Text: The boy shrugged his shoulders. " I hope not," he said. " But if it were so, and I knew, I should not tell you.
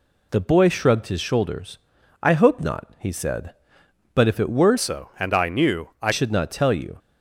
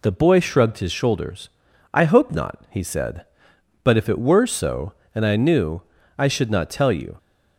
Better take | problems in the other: second | changes voice from "so" to "I"; from 4.7 to 6.1 s; 1.4 s long

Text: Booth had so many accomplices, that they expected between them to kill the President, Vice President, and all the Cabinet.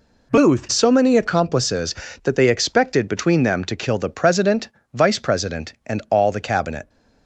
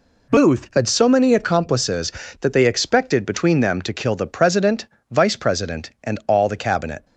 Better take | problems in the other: second | skips "had"; at 0.6 s

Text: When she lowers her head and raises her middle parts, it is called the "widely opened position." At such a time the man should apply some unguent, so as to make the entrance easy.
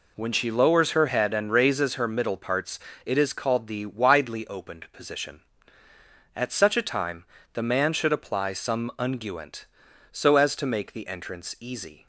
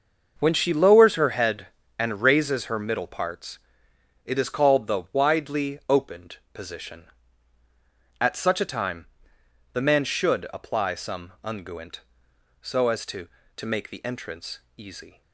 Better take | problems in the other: first | starts louder than the rest; noticeable; until 1.4 s; 6 dB // pauses between "opened" and "position"; slight; at 6.3 s; 0.16 s long // pauses between "time" and "the"; noticeable; at 9.0 s; 0.66 s long; slight in the first // says "to" twice; at 13.5 s // pauses between "entrance" and "easy"; slight; at 14.5 s; 0.18 s long

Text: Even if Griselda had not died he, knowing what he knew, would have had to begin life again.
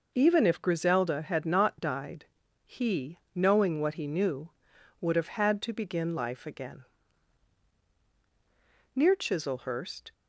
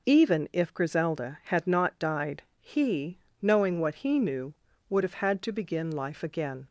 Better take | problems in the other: second | pauses between "died" and "he"; at 2.2 s; 0.38 s long; slight in the second // goes on to say "Near Chislehurst"; noticeable; from 8.9 s on; 1.1 s long

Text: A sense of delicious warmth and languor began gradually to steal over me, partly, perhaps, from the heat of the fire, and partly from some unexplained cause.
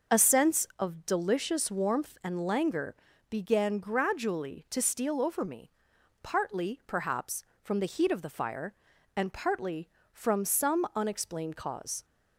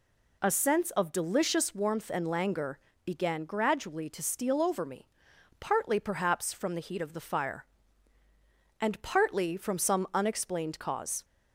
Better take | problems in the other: neither | pauses between "languor" and "began"; slight; the same in both

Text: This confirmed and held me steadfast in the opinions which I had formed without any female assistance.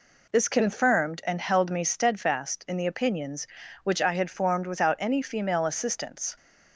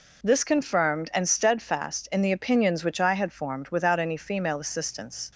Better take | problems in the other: first | skips "held me"; at 1.2 s

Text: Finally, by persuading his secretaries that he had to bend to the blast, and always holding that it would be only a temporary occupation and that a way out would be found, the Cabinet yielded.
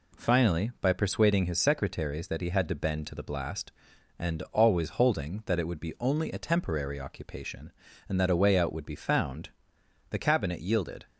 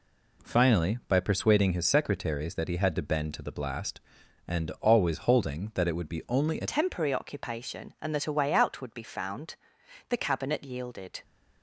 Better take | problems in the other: first | changes voice at "temporary"; from 6.6 s on; 4.6 s long

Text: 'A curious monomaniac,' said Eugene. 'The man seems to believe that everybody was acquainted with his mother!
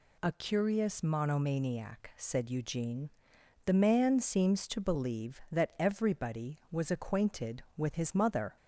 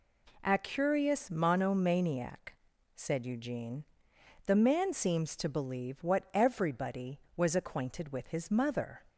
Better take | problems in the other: first | says "what" for "that"; at 6.0 s

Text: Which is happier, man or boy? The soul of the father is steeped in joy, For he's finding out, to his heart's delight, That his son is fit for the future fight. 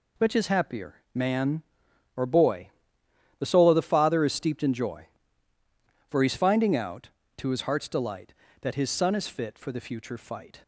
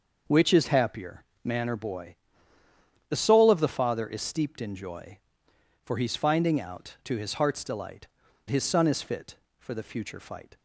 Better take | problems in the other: first | skips "That"; at 8.2 s

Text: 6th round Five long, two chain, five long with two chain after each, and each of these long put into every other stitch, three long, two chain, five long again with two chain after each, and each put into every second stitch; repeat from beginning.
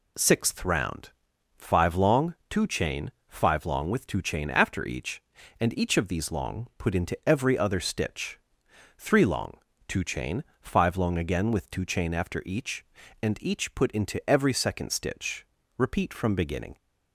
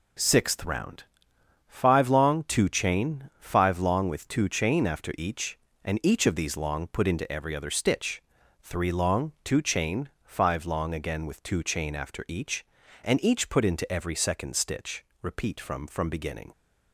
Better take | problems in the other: first | pauses between "round" and "Five"; noticeable; at 1.0 s; 0.64 s long; noticeable in the first // says "from" twice; at 15.8 s

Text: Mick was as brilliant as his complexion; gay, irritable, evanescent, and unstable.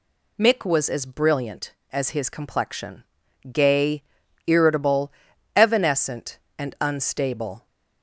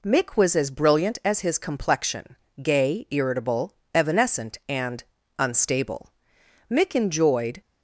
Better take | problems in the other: first | pauses between "and" and "unstable"; slight; at 5.0 s; 0.34 s long // goes on to say "Mick enjoyed"; noticeable; from 6.7 s on; 0.90 s long

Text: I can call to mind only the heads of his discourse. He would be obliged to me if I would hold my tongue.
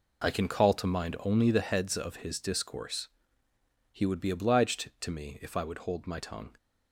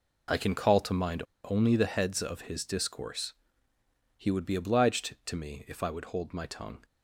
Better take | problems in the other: first | pauses between "mind" and "only"; slight; at 1.2 s; 0.20 s long

